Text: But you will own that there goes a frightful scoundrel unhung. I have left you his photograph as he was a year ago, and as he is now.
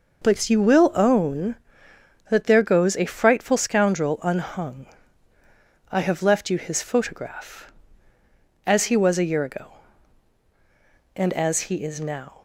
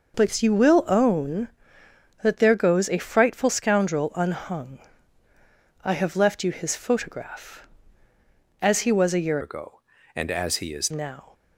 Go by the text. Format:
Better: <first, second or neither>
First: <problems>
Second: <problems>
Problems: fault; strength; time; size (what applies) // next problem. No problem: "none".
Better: first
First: none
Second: changes voice from "ago" to "is"; from 9.4 to 10.9 s; 1.5 s long